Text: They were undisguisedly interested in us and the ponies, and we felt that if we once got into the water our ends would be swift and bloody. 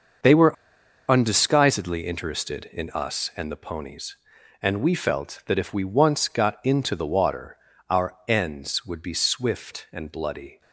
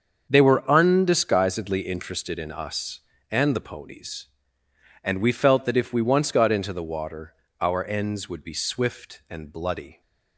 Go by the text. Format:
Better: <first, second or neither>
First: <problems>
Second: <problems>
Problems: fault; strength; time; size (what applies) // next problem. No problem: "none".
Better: second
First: starts louder than the rest; until 1.7 s; 6.5 dB // pauses between "were" and "undisguisedly"; noticeable; at 0.5 s; 0.55 s long // pauses between "water" and "our"; slight; at 7.5 s; 0.34 s long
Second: starts louder than the rest; until 1.3 s; 6.5 dB // pauses between "water" and "our"; slight; at 7.3 s; 0.26 s long